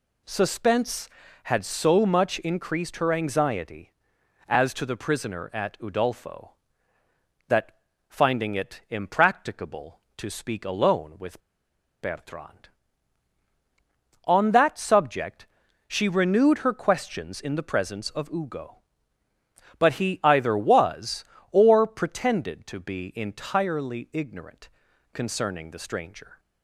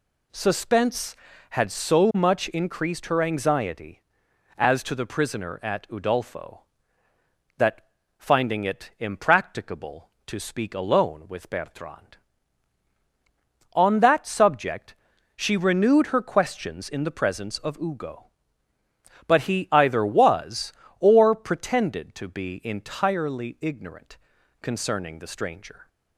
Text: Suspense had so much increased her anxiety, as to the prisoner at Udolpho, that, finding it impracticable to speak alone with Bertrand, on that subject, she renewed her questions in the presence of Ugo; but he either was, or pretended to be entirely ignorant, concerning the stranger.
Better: second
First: pauses between "with" and "Bertrand"; noticeable; at 11.4 s; 0.61 s long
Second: none

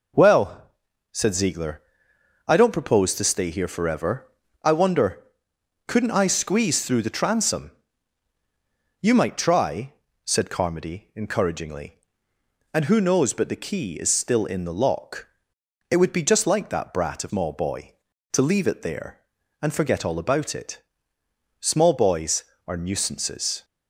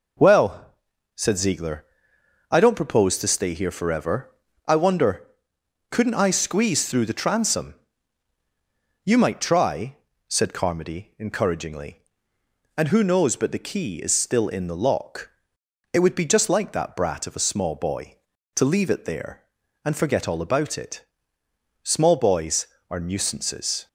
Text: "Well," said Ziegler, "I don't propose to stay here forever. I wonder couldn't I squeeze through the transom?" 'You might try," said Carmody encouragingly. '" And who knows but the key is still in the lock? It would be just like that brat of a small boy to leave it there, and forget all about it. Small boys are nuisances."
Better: second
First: pauses between "wonder" and "couldn't"; noticeable; at 5.2 s; 0.66 s long // skips "a"; at 17.2 s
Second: pauses between "wonder" and "couldn't"; noticeable; at 5.2 s; 0.66 s long

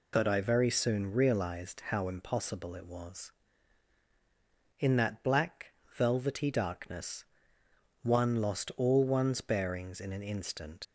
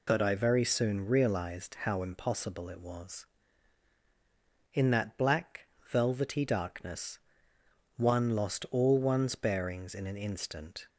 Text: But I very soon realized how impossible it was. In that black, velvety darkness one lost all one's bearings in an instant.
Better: second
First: pauses between "darkness" and "one"; noticeable; at 7.2 s; 0.80 s long // leaves "instant" unfinished; at 10.8 s; 95 ms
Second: pauses between "darkness" and "one"; noticeable; at 7.1 s; 0.80 s long

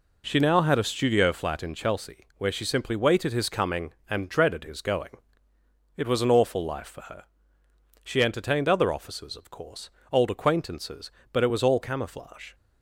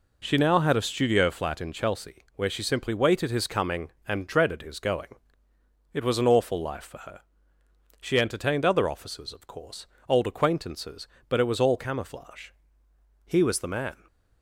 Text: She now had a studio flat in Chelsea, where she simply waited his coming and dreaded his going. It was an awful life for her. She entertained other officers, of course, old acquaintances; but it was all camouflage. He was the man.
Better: second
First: stops before "He was the man"; at 12.5 s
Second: none

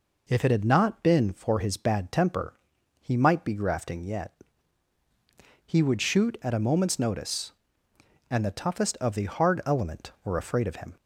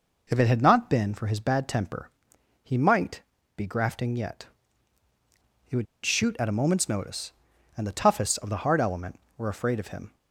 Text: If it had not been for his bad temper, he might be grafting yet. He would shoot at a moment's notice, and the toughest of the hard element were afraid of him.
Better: first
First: none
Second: pauses between "might" and "be"; slight; at 3.2 s; 0.34 s long // pauses between "would" and "shoot"; slight; at 5.8 s; 0.18 s long

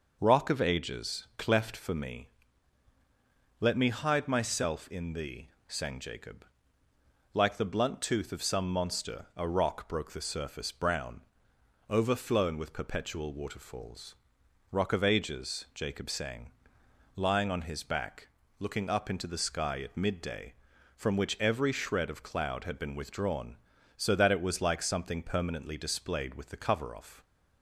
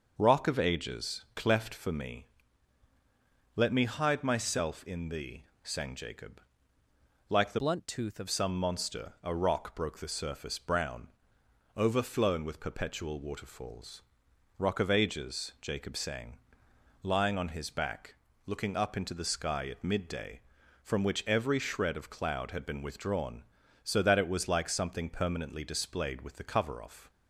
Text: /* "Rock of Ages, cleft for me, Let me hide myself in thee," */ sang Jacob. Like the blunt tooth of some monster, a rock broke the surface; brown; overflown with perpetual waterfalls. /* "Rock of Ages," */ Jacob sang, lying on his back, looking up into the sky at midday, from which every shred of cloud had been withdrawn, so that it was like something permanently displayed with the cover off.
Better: first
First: none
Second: starts louder than the rest; noticeable; until 1.1 s; 6 dB // changes voice from "blunt" to "of"; from 7.5 to 8.2 s; 0.7 s long

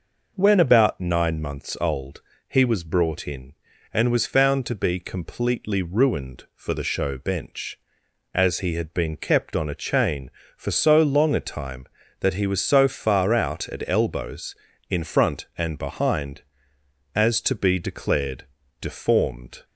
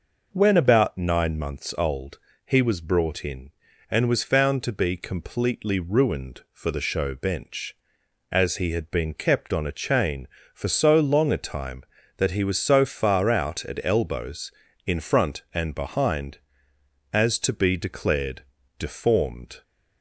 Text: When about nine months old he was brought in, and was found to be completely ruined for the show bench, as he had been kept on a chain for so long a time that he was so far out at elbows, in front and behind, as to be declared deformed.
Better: neither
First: pauses between "old" and "he"; slight; at 2.2 s; 0.26 s long // pauses between "declared" and "deformed"; slight; at 18.4 s; 0.34 s long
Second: pauses between "old" and "he"; slight; at 2.1 s; 0.26 s long // pauses between "declared" and "deformed"; slight; at 18.4 s; 0.34 s long

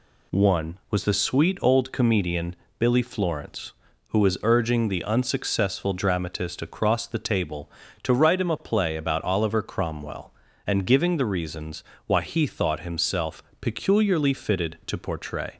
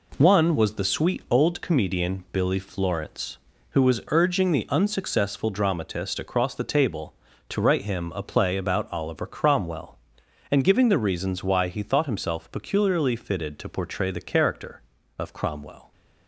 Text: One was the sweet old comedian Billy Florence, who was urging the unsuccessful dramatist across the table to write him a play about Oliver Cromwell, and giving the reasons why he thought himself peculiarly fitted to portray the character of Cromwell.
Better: second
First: pauses between "comedian" and "Billy"; slight; at 2.5 s; 0.24 s long // pauses between "reasons" and "why"; slight; at 11.8 s; 0.22 s long // pauses between "himself" and "peculiarly"; slight; at 13.4 s; 0.18 s long // stops before "the character of Cromwell"; at 15.5 s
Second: none

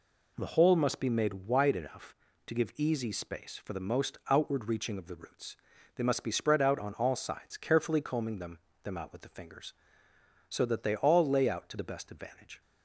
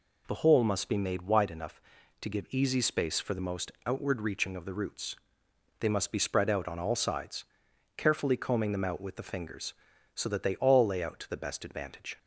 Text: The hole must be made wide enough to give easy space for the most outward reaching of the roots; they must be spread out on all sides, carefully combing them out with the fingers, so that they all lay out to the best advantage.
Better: second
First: says "them" twice; at 8.8 s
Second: none

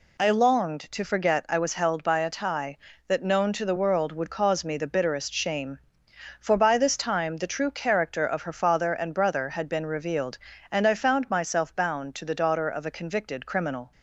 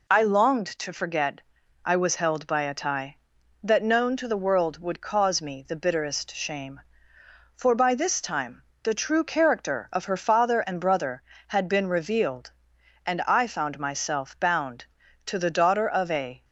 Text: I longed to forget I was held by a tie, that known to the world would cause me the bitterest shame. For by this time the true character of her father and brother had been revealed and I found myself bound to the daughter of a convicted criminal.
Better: first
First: none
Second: pauses between "forget" and "I"; at 1.4 s; 0.42 s long // pauses between "time" and "the"; slight; at 8.6 s; 0.20 s long // stops before "convicted criminal"; at 16.4 s

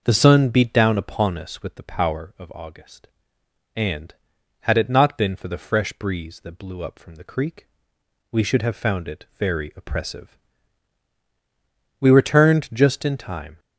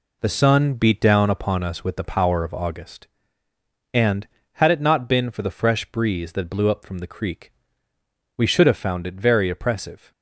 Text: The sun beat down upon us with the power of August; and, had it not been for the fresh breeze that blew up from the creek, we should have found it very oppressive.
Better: second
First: goes on to say "We returned just in time"; from 12.0 s on; 1.5 s long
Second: none

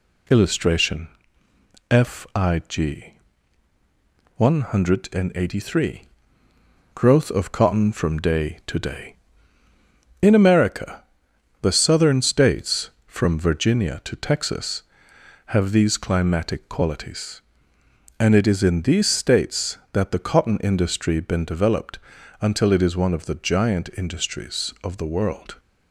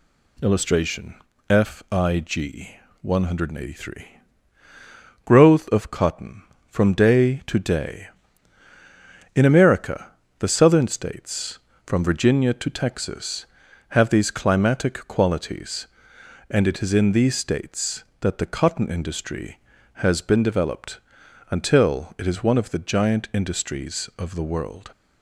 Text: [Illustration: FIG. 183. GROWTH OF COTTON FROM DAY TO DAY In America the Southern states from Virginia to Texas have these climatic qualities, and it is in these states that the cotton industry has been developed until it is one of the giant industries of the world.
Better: second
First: pauses between "America" and "the"; noticeable; at 11.0 s; 0.58 s long // skips "has"; at 21.1 s // pauses between "developed" and "until"; at 21.9 s; 0.44 s long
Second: pauses between "America" and "the"; slight; at 10.1 s; 0.26 s long // pauses between "developed" and "until"; noticeable; at 20.9 s; 0.50 s long

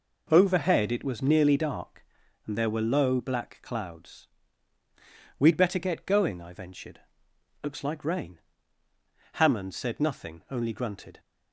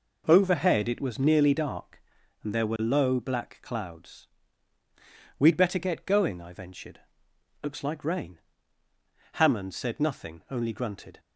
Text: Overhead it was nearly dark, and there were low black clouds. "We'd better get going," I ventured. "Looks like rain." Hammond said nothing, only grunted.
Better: neither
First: none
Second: none

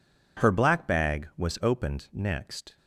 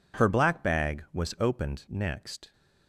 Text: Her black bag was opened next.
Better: neither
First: none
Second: none

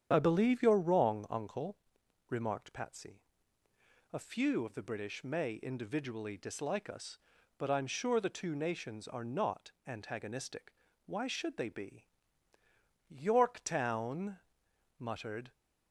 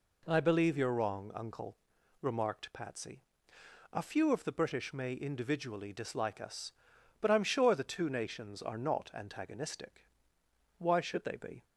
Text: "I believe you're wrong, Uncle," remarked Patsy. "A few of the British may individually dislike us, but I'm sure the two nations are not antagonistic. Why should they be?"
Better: second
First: starts louder than the rest; strong; until 1.1 s; 9 dB // goes on to say "Yorktown muttered"; strong; from 13.0 s on; 2.4 s long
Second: none

